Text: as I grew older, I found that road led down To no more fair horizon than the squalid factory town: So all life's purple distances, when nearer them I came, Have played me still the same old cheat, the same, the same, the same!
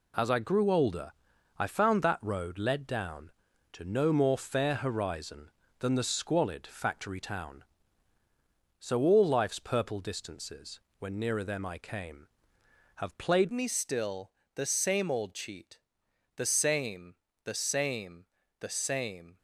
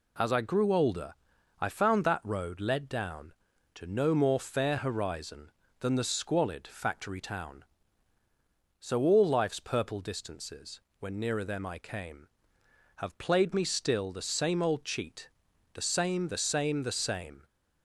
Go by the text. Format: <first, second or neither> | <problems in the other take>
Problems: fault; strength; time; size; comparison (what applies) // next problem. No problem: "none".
second | changes voice at "me"; from 13.5 s on; 5.8 s long // pauses between "still" and "the"; slight; at 14.3 s; 0.24 s long